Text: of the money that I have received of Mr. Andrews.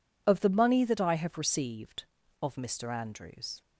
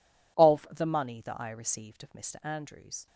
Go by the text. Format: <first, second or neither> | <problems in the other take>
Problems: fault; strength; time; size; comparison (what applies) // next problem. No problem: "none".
first | skips "have"; at 1.5 s